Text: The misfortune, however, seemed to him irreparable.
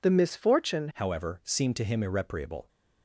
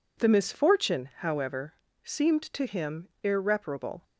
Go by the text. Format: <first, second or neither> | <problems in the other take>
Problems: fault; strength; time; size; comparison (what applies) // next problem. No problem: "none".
second | changes voice at "however"; from 0.9 s on; 1.7 s long